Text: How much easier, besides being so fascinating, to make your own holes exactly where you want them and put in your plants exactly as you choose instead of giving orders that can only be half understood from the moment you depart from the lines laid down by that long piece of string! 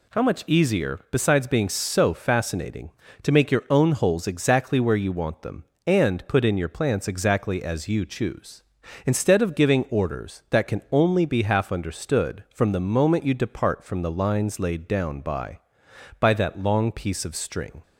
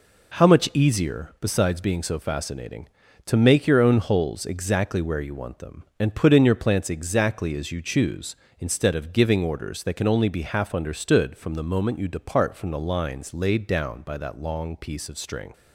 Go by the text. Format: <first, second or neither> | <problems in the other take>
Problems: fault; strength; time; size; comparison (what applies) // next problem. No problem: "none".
second | says "by" twice; at 16.1 s